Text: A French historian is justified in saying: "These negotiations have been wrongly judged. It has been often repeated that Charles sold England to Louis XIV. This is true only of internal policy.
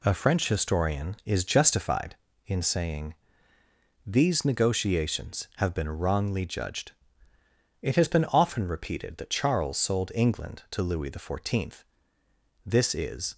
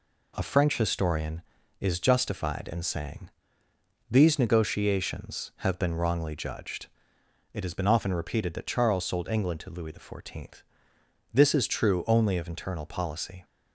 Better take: second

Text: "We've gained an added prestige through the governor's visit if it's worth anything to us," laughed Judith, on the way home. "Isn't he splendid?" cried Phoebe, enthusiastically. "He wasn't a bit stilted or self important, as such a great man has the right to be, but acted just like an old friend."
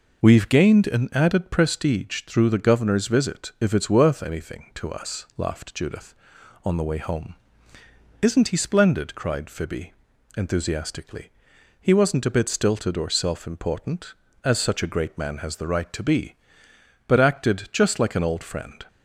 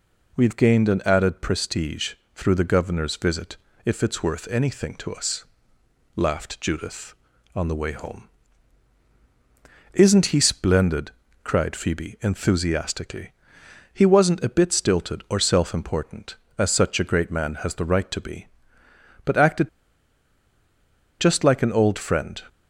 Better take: first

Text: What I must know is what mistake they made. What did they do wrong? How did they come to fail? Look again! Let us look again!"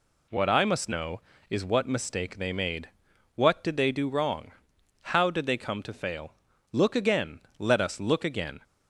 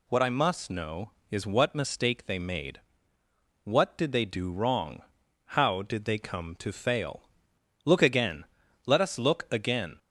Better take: neither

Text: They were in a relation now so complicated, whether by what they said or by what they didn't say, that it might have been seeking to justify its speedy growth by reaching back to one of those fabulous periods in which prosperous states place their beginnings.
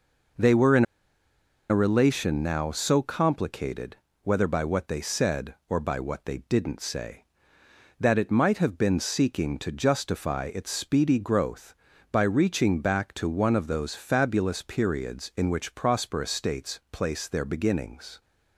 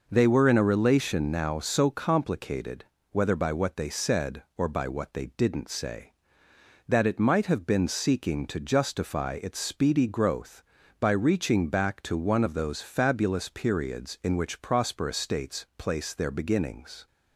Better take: second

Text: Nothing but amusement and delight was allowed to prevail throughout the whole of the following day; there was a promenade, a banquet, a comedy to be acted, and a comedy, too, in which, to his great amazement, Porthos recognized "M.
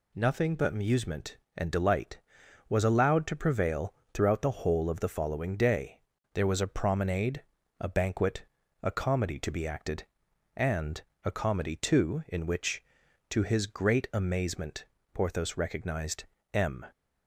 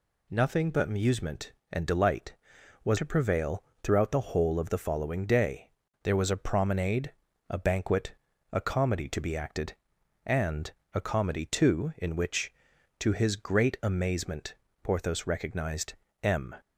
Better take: first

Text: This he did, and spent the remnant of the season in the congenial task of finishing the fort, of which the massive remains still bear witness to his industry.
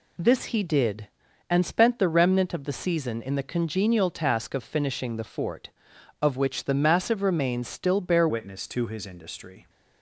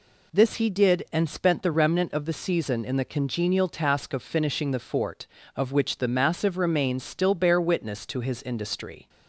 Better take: second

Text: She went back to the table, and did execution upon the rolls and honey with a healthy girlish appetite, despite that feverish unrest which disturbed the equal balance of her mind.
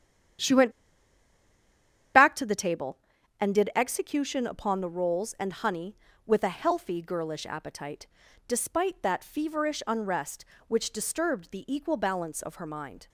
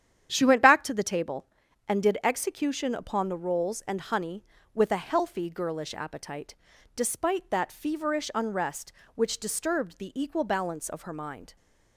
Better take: second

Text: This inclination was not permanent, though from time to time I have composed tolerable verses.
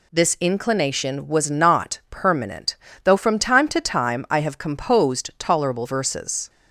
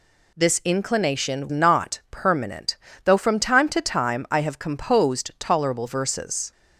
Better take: first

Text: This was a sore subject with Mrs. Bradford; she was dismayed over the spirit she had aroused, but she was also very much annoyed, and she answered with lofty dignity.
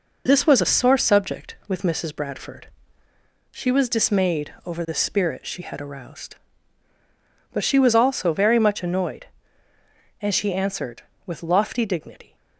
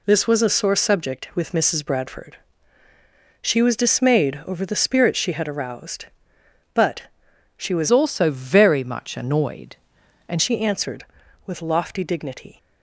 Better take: first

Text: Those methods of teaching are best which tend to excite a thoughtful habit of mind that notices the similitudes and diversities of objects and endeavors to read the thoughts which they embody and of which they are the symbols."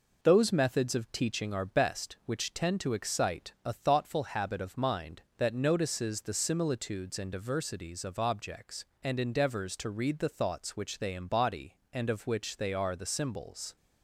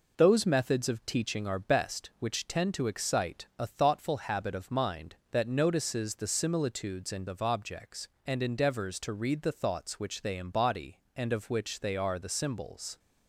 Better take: first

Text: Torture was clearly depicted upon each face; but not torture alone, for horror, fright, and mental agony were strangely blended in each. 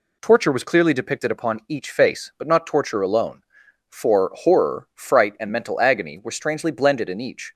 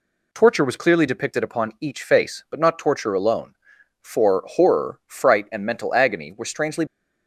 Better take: first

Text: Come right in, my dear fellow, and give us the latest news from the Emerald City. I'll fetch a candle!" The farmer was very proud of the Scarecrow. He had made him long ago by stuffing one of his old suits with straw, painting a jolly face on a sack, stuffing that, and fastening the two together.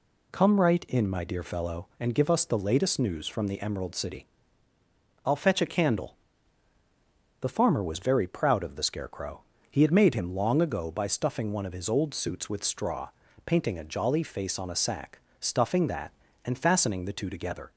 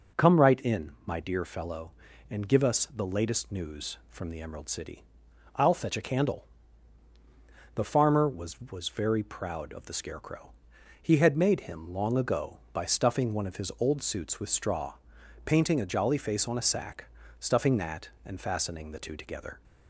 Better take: first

